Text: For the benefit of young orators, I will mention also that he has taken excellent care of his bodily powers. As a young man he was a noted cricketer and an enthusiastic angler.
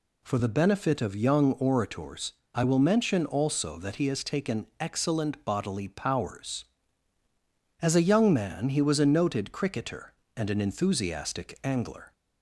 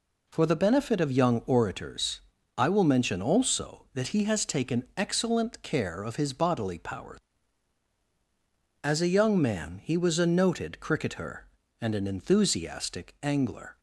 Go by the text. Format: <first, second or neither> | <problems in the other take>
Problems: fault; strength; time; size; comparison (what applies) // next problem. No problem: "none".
second | skips "care of his"; at 5.4 s